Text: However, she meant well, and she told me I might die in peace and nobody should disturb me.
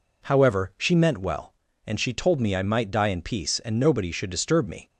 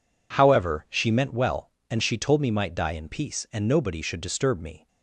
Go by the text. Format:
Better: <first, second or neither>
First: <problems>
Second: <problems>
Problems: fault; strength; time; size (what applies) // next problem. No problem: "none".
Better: first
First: none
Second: skips "I"; at 2.4 s